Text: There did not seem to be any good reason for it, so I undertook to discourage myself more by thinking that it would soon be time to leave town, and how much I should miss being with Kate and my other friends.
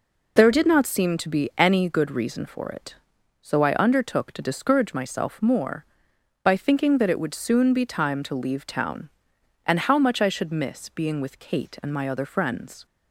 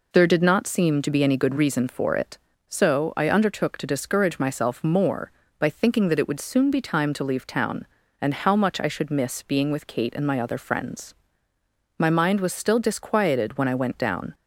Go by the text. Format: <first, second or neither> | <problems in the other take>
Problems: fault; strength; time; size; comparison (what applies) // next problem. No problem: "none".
first | goes on to say "My mind was still disquieted when I went down"; strong; from 11.9 s on; 2.3 s long